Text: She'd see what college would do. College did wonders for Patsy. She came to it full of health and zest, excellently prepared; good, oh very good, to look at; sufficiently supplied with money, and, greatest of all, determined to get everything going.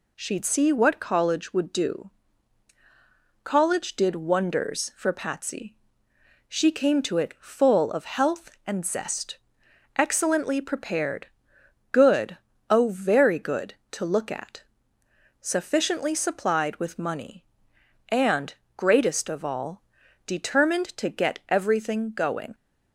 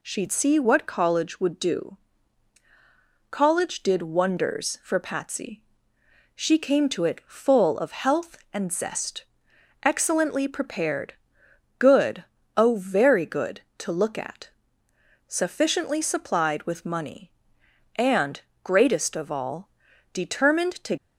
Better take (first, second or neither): first